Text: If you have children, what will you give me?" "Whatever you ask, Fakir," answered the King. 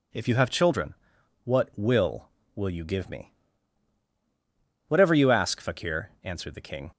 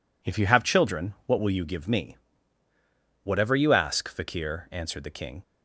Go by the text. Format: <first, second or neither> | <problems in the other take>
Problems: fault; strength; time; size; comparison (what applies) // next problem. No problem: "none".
second | says "will" twice; at 2.5 s